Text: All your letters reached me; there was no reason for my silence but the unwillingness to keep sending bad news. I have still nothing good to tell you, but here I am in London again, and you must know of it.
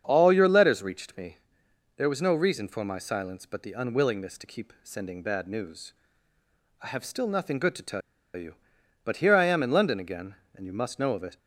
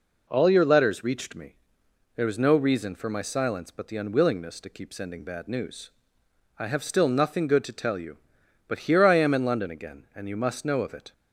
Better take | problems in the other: second | starts louder than the rest; strong; until 1.0 s; 7.5 dB // pauses between "tell" and "you"; slight; at 8.0 s; 0.35 s long

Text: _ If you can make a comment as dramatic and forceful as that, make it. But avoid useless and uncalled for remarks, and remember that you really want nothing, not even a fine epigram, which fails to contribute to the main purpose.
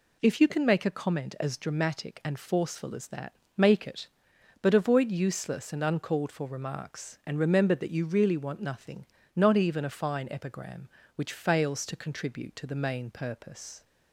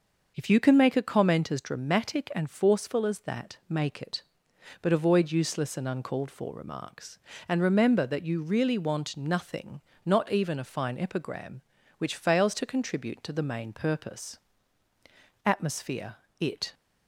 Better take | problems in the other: first | starts louder than the rest; noticeable; until 1.3 s; 6 dB // goes on to say "Atmosphere It"; noticeable; from 15.4 s on; 1.3 s long

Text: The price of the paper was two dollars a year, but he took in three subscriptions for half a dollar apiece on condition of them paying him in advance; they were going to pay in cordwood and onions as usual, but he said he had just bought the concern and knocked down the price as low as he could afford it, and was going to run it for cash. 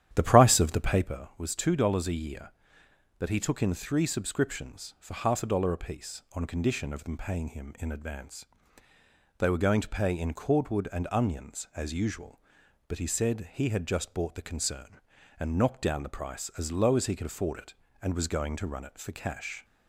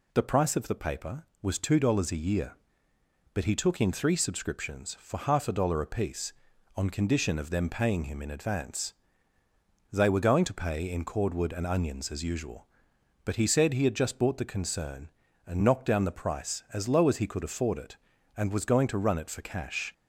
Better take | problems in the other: second | starts louder than the rest; strong; until 1.1 s; 10.5 dB

